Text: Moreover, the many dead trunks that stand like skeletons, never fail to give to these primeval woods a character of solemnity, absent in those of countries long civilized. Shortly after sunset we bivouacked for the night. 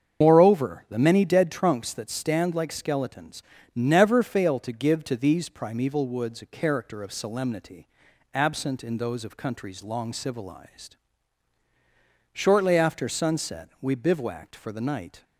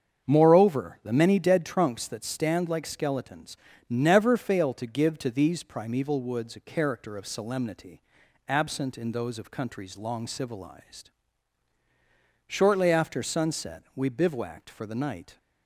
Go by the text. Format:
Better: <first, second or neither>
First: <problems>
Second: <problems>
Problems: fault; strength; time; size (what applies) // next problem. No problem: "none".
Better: second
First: loses the start of "Moreover"; at 0.2 s; 95 ms // starts louder than the rest; strong; until 1.2 s; 7.5 dB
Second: starts louder than the rest; strong; until 1.3 s; 7.5 dB